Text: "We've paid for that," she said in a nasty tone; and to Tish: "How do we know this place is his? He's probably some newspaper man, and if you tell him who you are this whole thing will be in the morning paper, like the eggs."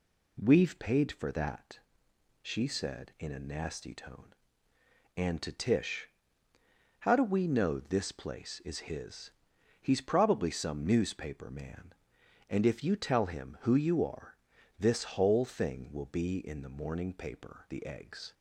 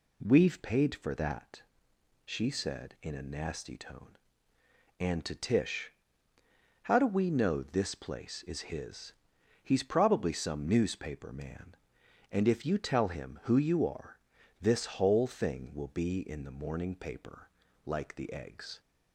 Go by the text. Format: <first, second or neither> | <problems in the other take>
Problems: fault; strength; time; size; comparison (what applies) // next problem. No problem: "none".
second | pauses between "are" and "this"; at 14.3 s; 0.42 s long; also in the second // skips "like"; at 17.6 s